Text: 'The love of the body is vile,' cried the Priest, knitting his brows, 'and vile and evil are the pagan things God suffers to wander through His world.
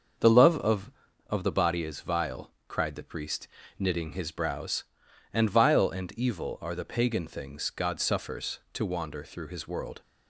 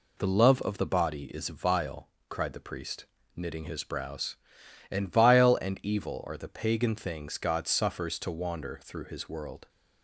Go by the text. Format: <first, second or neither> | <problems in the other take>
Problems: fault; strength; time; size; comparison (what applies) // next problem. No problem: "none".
second | starts louder than the rest; until 1.5 s; 6.5 dB // says "of" twice; at 1.2 s